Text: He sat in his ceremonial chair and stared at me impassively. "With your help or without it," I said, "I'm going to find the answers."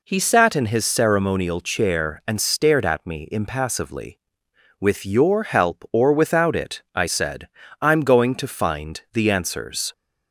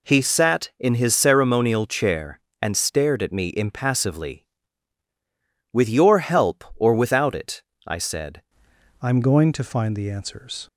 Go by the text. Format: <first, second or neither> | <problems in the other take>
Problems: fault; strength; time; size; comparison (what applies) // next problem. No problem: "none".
first | changes voice at "I'm"; from 9.0 s on; 1.6 s long